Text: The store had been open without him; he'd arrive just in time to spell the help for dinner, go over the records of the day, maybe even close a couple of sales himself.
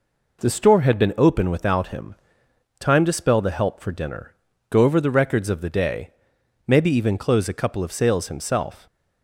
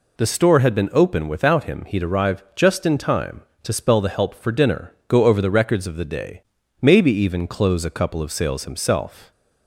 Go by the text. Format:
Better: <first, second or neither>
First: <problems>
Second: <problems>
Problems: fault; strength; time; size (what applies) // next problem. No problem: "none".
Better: second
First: skips "he'd arrive just in"; at 2.4 s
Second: none